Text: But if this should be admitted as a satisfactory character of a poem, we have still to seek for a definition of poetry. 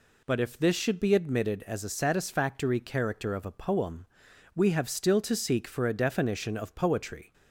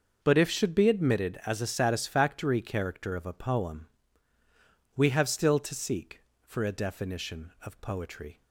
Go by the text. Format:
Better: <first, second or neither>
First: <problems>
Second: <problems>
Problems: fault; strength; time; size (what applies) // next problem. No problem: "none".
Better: first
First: none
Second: starts louder than the rest; until 1.2 s; 6 dB // skips "this"; at 0.4 s